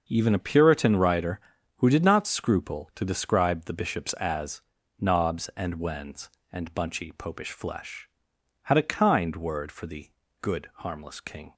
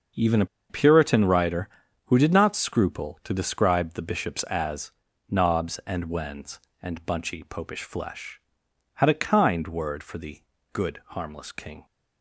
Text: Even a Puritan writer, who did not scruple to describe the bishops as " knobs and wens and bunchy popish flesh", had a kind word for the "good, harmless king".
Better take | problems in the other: first | starts louder than the rest; until 1.4 s; 6 dB; noticeable in the first // pauses between "a" and "Puritan"; slight; at 0.4 s; 0.24 s long // pauses between "the" and "good"; slight; at 10.4 s; 0.32 s long; slight in the first

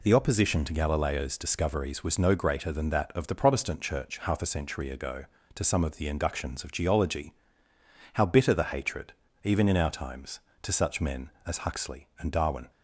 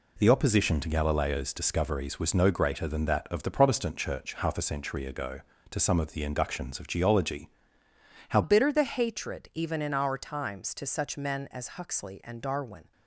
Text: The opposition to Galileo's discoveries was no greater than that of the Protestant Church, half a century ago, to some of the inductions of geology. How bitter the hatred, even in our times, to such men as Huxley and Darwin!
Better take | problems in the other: first | changes voice at "bitter"; from 8.4 s on; 4.5 s long

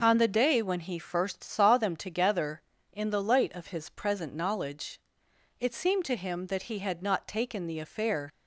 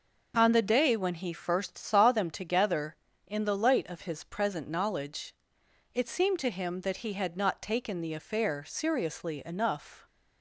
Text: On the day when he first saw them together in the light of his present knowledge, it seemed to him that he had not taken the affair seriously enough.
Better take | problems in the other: second | stops before "seriously enough"; at 8.3 s

